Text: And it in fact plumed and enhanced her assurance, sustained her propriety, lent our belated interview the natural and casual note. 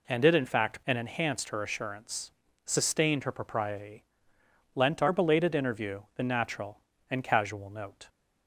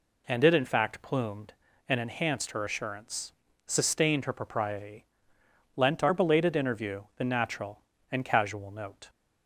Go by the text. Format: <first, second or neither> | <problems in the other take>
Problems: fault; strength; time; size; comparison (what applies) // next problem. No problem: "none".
second | skips "plumed"; at 0.8 s